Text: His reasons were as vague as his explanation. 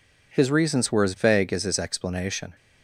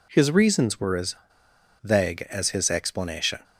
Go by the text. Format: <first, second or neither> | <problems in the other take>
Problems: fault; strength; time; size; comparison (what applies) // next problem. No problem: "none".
first | pauses between "as" and "vague"; noticeable; at 1.1 s; 0.67 s long